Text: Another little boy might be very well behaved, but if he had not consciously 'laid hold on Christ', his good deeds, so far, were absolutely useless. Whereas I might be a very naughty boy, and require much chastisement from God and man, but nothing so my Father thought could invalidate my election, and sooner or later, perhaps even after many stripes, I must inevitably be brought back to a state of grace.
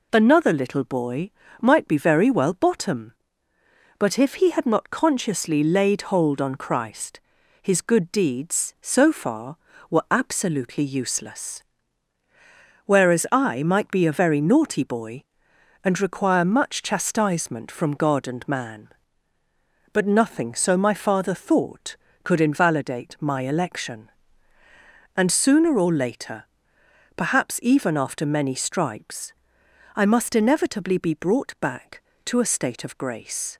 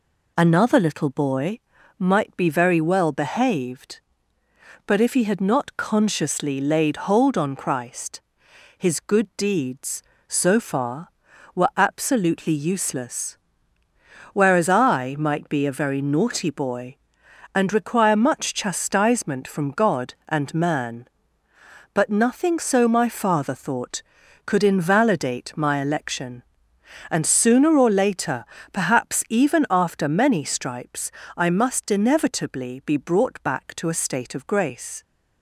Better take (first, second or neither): second